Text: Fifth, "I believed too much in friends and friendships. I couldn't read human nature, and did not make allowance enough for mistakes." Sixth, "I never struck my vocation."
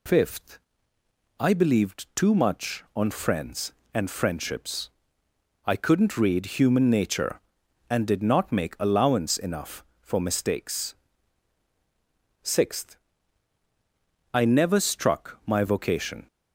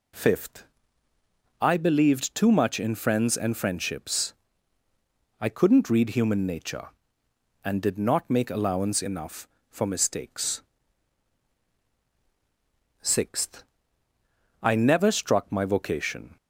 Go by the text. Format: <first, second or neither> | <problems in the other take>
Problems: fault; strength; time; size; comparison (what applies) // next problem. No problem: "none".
second | says "on" for "in"; at 2.9 s